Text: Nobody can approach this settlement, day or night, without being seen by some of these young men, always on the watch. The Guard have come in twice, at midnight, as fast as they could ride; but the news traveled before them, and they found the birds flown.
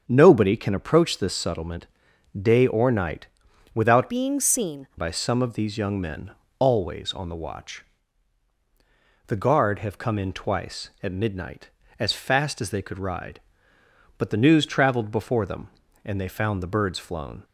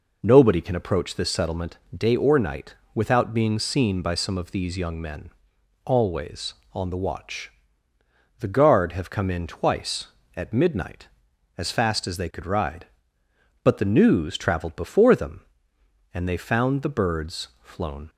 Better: second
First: starts louder than the rest; strong; until 1.0 s; 7.5 dB // changes voice from "being" to "seen"; from 4.0 to 4.8 s; 0.8 s long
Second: none

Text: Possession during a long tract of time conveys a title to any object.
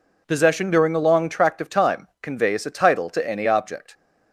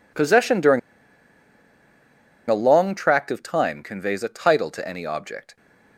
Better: first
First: none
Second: pauses between "during" and "a"; strong; at 0.7 s; 1.6 s long

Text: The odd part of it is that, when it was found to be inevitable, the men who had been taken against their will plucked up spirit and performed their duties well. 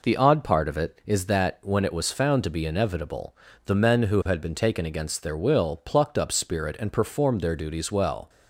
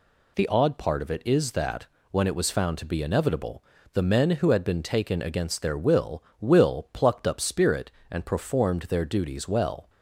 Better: first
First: none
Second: says "will" twice; at 6.3 s

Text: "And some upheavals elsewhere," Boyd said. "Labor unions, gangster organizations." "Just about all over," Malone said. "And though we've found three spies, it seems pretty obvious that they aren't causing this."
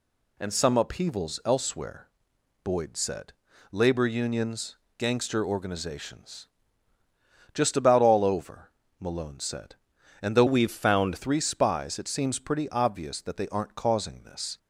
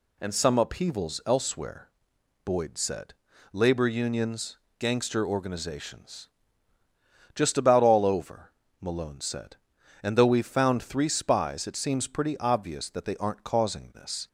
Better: second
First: changes voice from "we've" to "found"; from 10.4 to 11.1 s; 0.7 s long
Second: none

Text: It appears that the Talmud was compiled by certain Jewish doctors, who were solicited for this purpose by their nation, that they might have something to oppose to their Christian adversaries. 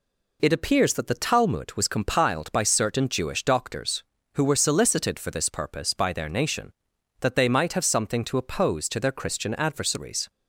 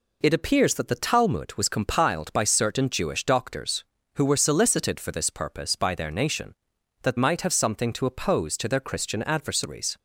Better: first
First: none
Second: skips "they"; at 7.1 s

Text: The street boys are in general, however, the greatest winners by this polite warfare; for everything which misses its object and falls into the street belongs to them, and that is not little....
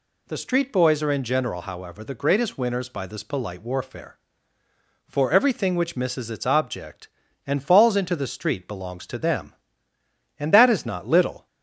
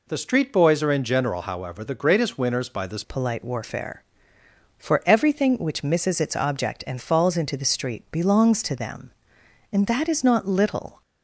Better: first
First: none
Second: changes voice at "polite"; from 3.0 s on; 8.0 s long

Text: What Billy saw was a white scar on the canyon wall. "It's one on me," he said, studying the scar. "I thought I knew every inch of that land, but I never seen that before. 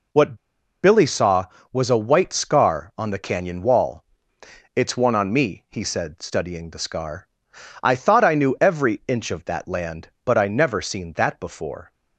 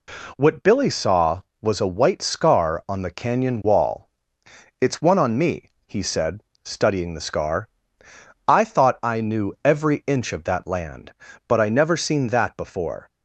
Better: second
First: pauses between "What" and "Billy"; noticeable; at 0.3 s; 0.48 s long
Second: none

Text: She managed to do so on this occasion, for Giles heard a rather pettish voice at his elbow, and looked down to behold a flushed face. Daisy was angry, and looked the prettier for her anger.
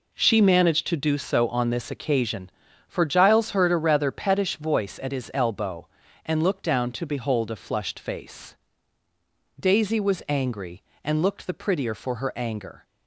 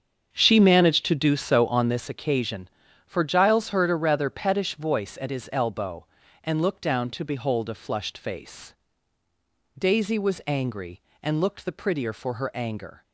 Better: first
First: none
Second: starts louder than the rest; strong; until 2.1 s; 7 dB

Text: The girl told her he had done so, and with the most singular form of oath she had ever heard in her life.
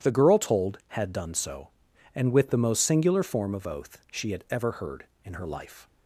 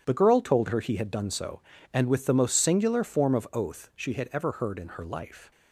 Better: second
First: skips "her he"; at 0.8 s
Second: none

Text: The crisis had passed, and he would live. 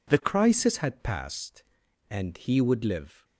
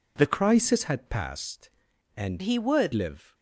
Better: first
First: none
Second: changes voice from "he" to "would"; from 2.4 to 2.9 s; 0.5 s long

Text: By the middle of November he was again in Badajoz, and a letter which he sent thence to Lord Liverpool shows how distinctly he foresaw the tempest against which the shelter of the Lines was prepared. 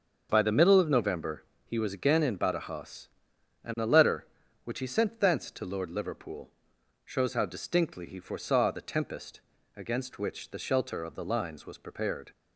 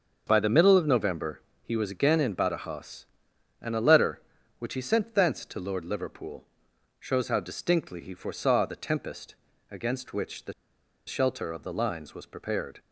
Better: first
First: starts louder than the rest; until 1.3 s; 6.5 dB // pauses between "November" and "he"; slight; at 1.4 s; 0.22 s long // pauses between "Liverpool" and "shows"; noticeable; at 6.4 s; 0.56 s long // pauses between "tempest" and "against"; slight; at 9.4 s; 0.34 s long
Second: starts louder than the rest; until 1.2 s; 6.5 dB // pauses between "November" and "he"; slight; at 1.3 s; 0.22 s long // pauses between "Liverpool" and "shows"; noticeable; at 6.4 s; 0.56 s long // pauses between "tempest" and "against"; slight; at 9.3 s; 0.34 s long // pauses between "the" and "shelter"; noticeable; at 10.5 s; 0.55 s long

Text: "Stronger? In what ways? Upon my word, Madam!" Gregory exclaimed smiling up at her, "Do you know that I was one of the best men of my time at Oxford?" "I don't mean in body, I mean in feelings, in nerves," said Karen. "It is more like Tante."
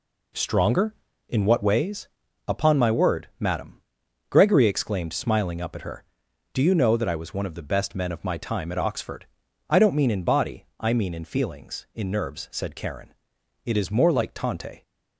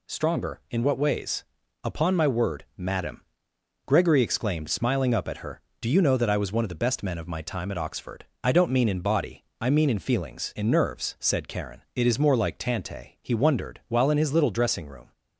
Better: first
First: none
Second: goes on to say "He wondered while in his little dressing room"; strong; from 13.2 s on; 1.9 s long

